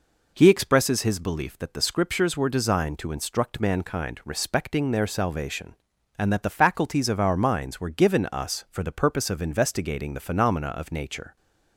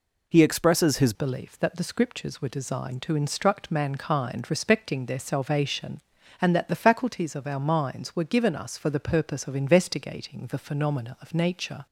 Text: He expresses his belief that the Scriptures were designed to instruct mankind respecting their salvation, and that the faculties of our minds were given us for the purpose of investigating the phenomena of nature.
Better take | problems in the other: first | changes voice at "belief"; from 1.1 s on; 10.7 s long

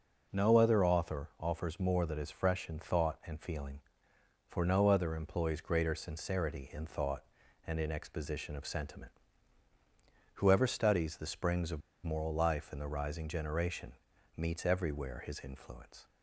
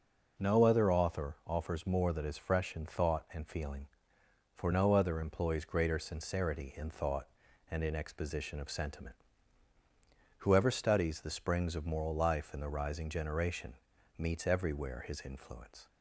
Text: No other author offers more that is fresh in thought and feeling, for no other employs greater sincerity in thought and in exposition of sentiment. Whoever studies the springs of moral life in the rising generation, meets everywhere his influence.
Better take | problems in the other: second | pauses between "of" and "moral"; slight; at 11.8 s; 0.23 s long

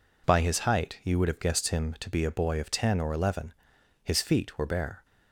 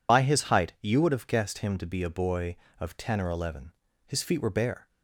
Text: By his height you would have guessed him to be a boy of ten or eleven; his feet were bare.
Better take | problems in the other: first | loses the start of "By"; at 0.0 s; 65 ms

